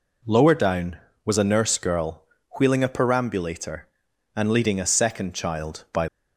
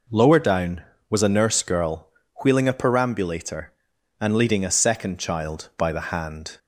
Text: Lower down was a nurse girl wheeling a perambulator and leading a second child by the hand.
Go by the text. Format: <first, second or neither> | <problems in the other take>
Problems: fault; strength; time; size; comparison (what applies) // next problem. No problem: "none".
second | pauses between "girl" and "wheeling"; at 2.2 s; 0.38 s long; also in the second // stops before "the hand"; at 6.0 s